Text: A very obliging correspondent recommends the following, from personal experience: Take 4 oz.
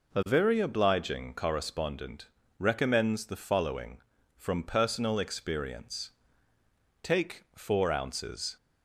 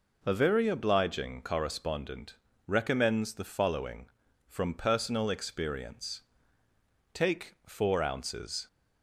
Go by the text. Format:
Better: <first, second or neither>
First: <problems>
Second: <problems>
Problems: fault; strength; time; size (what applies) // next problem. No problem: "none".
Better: neither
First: pauses between "correspondent" and "recommends"; slight; at 2.2 s; 0.34 s long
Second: pauses between "correspondent" and "recommends"; slight; at 2.3 s; 0.34 s long